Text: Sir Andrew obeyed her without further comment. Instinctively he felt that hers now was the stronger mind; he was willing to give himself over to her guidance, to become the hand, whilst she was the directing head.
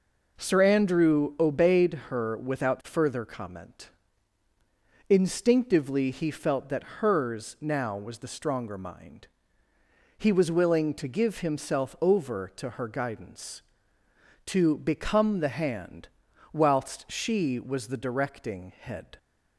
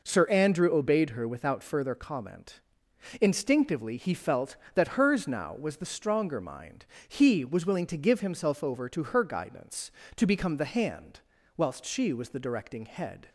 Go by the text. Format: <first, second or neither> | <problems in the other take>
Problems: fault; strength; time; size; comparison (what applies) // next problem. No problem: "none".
neither | none